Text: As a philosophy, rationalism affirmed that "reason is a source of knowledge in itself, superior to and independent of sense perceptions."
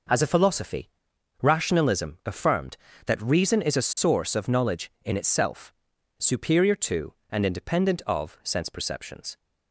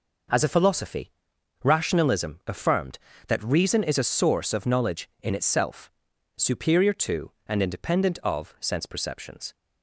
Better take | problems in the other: neither | none

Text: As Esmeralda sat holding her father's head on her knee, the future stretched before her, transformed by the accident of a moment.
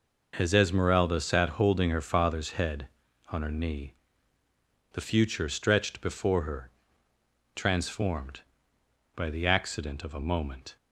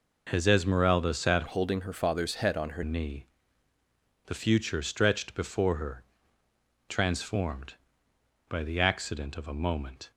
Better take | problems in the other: first | changes voice from "holding" to "her"; from 1.4 to 2.8 s; 1.4 s long

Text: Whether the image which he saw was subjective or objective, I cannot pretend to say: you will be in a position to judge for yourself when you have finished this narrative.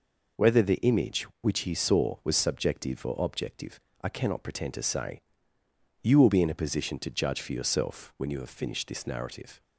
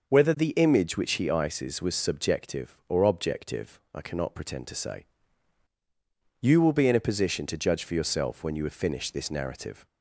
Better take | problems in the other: first | says "ices" for "saw"; at 1.2 s

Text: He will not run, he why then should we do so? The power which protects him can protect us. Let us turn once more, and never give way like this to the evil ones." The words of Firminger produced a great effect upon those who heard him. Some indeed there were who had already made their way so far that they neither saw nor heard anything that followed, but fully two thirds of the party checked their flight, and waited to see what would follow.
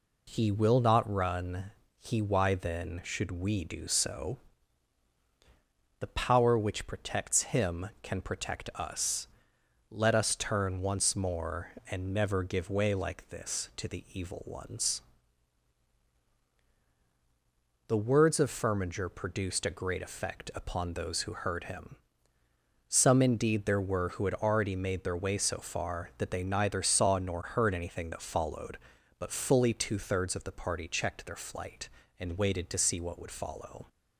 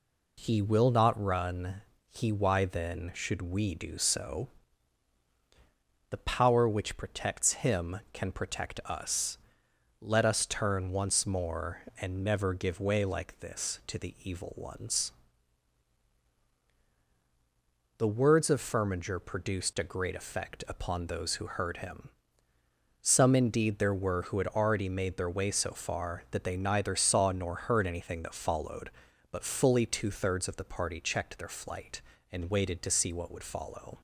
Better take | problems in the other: neither | none

